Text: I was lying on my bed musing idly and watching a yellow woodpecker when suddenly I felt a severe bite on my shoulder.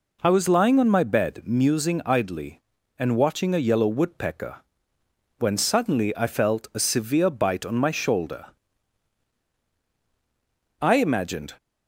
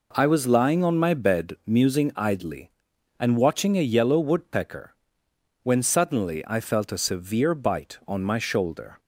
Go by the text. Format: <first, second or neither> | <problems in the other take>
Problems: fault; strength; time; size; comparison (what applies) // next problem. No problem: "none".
second | pauses between "woodpecker" and "when"; noticeable; at 4.5 s; 0.82 s long; noticeable in the second // goes on to say "I imagined"; noticeable; from 10.8 s on; 0.74 s long